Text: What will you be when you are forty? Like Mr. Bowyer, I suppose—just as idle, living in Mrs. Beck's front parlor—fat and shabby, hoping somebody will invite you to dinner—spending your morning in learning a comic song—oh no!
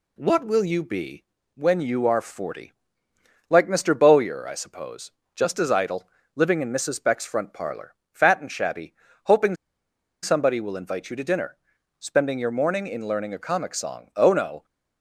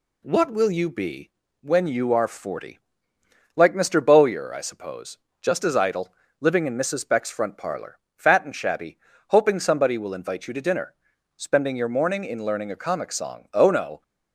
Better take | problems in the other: second | pauses between "be" and "when"; slight; at 1.2 s; 0.32 s long; slight in the second // pauses between "hoping" and "somebody"; noticeable; at 9.5 s; 0.68 s long

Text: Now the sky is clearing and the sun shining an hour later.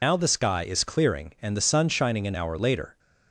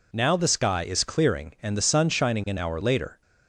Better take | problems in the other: second | loses the start of "Now"; at 0.0 s; 90 ms

